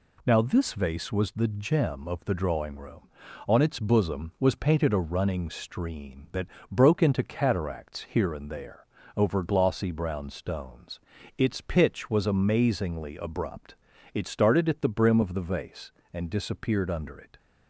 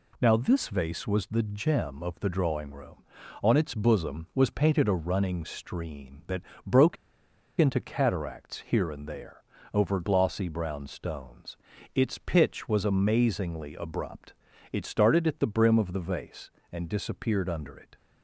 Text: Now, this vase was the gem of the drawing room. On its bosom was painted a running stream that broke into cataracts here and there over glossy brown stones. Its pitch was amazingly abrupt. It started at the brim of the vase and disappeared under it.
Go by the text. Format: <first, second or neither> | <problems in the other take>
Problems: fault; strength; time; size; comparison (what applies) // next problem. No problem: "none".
first | pauses between "that" and "broke"; slight; at 6.4 s; 0.24 s long; slight in the first // pauses between "broke" and "into"; noticeable; at 6.9 s; 0.64 s long // pauses between "there" and "over"; slight; at 9.4 s; 0.30 s long; slight in the first